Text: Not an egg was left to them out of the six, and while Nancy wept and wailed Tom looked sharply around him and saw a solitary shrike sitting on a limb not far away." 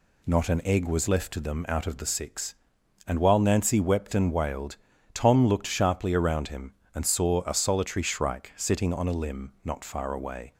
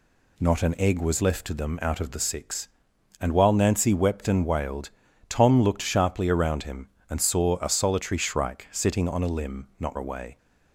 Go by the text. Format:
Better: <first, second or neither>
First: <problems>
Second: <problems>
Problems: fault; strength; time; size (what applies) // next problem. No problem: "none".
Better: first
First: pauses between "wailed" and "Tom"; at 4.7 s; 0.38 s long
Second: pauses between "wailed" and "Tom"; at 4.9 s; 0.38 s long // skips "far"; at 9.9 s